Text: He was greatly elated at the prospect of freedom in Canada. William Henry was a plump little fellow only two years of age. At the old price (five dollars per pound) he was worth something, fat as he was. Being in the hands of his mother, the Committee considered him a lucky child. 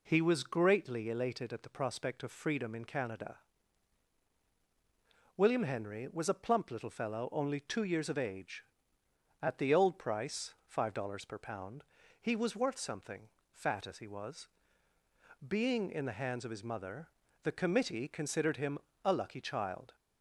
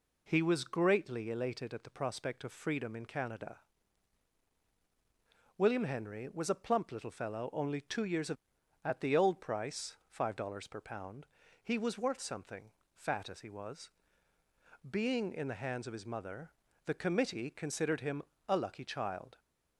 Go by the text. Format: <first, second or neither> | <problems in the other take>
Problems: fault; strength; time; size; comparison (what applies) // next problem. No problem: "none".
first | skips "age"; at 8.6 s // pauses between "him" and "a"; slight; at 18.2 s; 0.26 s long; slight in the first